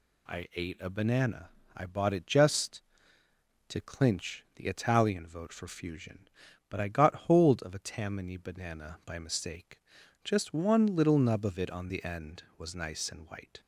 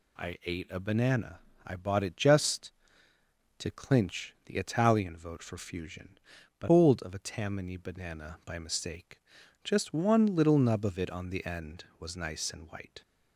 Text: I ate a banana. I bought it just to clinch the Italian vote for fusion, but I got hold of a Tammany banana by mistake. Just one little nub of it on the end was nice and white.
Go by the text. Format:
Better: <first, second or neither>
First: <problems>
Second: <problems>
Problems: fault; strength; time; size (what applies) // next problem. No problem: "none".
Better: first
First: none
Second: skips "I got"; at 6.6 s